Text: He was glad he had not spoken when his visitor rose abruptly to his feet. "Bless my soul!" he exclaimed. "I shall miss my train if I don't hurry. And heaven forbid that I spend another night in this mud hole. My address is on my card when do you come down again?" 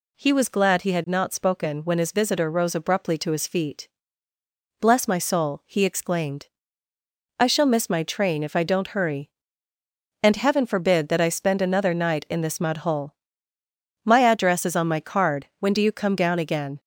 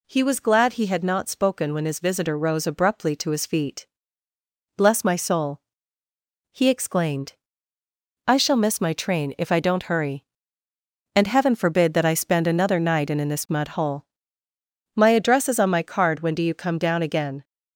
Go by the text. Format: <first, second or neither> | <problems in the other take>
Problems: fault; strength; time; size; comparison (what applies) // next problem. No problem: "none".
first | says "in" twice; at 13.1 s